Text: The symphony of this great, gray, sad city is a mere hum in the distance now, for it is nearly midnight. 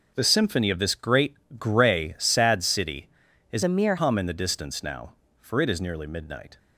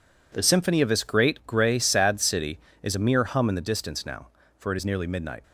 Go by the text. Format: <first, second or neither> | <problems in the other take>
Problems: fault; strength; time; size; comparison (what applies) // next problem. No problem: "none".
second | starts louder than the rest; noticeable; until 1.1 s; 6 dB // changes voice from "a" to "mere"; from 3.6 to 3.9 s; 0.3 s long